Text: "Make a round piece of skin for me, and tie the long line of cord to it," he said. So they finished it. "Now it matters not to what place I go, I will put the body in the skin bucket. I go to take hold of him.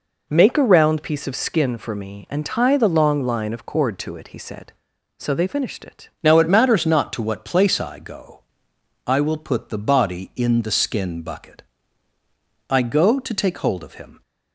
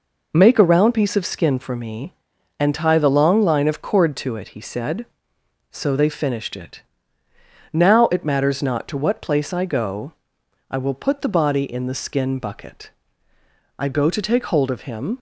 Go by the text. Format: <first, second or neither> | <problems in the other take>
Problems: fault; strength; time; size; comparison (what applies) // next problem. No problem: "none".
second | changes voice at "Now"; from 6.2 s on; 8.0 s long